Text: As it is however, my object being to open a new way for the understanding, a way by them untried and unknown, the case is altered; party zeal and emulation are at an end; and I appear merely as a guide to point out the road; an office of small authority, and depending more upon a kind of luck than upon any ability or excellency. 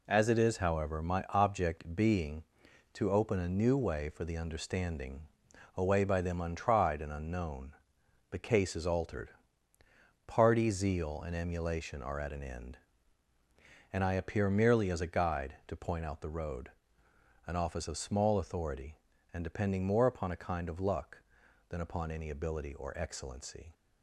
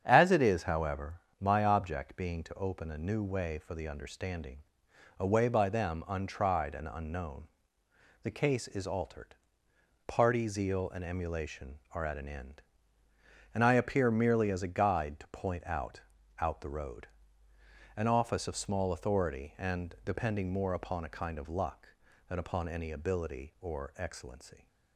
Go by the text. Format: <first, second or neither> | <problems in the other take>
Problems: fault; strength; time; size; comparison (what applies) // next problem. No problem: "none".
first | starts louder than the rest; strong; until 1.0 s; 8 dB // says "out" twice; at 16.3 s